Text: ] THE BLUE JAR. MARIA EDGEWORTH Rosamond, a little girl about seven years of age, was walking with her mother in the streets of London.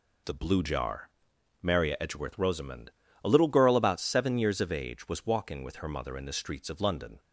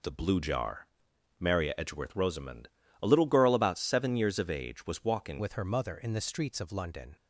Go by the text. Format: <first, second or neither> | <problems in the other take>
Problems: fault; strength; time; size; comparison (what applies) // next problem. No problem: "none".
first | changes voice at "with"; from 5.3 s on; 1.8 s long